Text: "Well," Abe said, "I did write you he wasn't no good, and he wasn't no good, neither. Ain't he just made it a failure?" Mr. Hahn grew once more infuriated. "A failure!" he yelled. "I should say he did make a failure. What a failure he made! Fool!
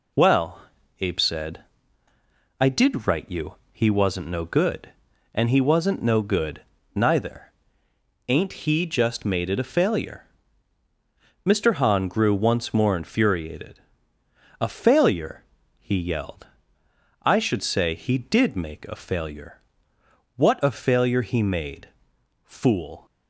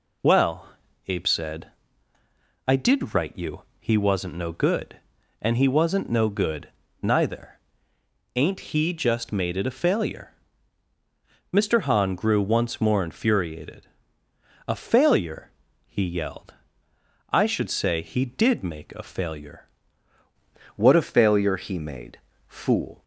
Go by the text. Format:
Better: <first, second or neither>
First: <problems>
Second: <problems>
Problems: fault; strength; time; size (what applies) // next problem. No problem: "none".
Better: first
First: pauses between "you" and "he"; slight; at 3.5 s; 0.18 s long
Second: pauses between "you" and "he"; slight; at 3.6 s; 0.18 s long // changes voice at "What"; from 20.7 s on; 2.3 s long